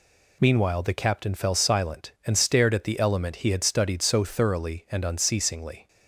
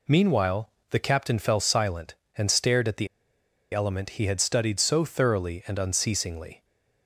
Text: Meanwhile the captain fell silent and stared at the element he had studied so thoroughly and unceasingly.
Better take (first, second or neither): first